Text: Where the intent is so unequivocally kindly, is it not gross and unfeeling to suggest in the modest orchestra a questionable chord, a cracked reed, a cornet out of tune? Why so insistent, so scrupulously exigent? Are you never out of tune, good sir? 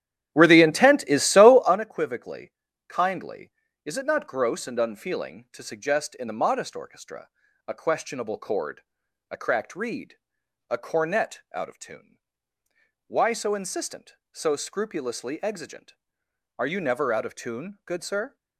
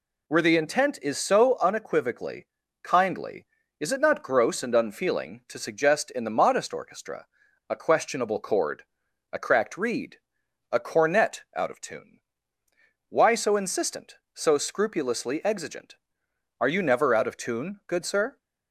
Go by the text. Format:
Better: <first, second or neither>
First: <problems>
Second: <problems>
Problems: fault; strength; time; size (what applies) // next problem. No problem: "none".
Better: second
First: starts louder than the rest; strong; until 1.8 s; 11 dB // pauses between "unequivocally" and "kindly"; slight; at 2.5 s; 0.34 s long // pauses between "orchestra" and "a"; at 7.2 s; 0.38 s long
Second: pauses between "unequivocally" and "kindly"; slight; at 2.4 s; 0.34 s long // pauses between "orchestra" and "a"; at 7.2 s; 0.42 s long